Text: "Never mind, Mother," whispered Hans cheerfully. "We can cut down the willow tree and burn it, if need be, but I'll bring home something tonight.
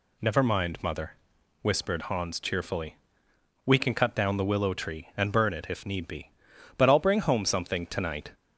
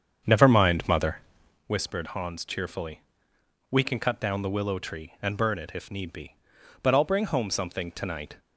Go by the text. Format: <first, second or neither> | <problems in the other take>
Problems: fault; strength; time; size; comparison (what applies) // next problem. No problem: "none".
first | starts louder than the rest; strong; until 1.6 s; 7.5 dB